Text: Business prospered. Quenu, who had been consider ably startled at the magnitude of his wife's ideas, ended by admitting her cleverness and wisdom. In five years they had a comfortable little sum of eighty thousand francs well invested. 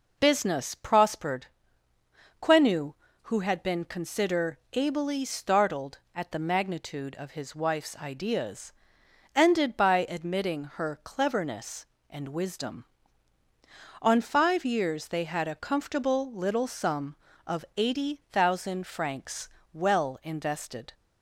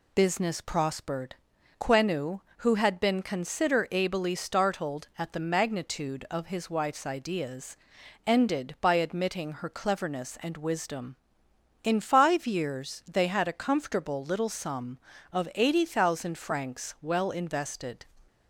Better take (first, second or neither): second